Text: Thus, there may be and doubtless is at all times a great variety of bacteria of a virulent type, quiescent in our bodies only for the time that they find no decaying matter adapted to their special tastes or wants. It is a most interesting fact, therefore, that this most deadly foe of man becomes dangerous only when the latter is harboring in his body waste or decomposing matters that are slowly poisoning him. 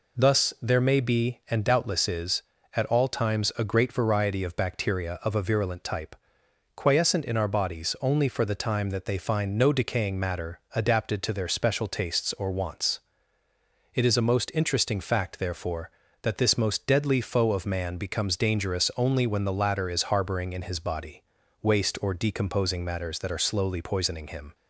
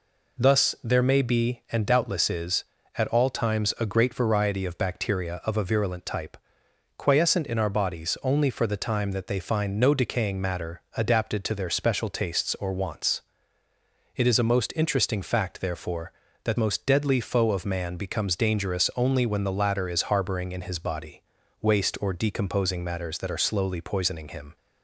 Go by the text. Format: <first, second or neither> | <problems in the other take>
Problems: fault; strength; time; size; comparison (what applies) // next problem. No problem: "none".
first | skips "this"; at 16.5 s // pauses between "body" and "waste"; at 21.2 s; 0.40 s long; also in the first